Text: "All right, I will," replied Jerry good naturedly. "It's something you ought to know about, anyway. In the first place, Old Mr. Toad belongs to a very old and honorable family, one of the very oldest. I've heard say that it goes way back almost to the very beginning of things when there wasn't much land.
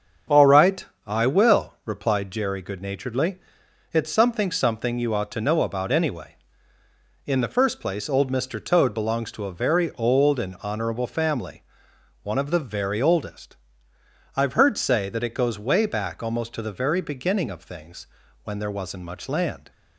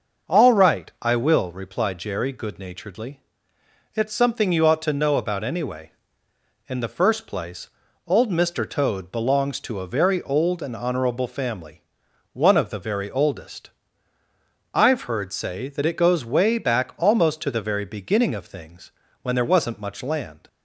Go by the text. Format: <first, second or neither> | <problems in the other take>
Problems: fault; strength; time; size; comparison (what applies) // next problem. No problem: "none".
second | starts louder than the rest; strong; until 1.5 s; 7 dB; noticeable in the second // says "something" twice; at 4.5 s // pauses between "things" and "when"; at 18.0 s; 0.40 s long; slight in the second